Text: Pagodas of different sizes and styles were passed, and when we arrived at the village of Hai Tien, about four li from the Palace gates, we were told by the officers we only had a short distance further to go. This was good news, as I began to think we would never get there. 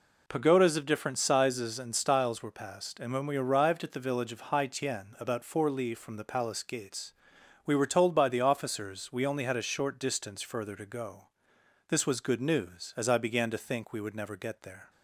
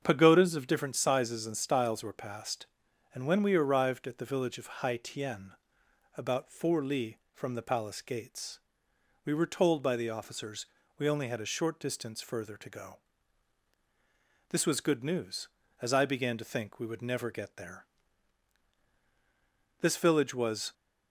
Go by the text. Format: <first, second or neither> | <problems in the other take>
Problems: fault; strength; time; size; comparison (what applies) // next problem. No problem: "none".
first | starts louder than the rest; strong; until 1.0 s; 7 dB // pauses between "officers" and "we"; slight; at 10.6 s; 0.34 s long // goes on to say "This village was"; noticeable; from 19.7 s on; 0.94 s long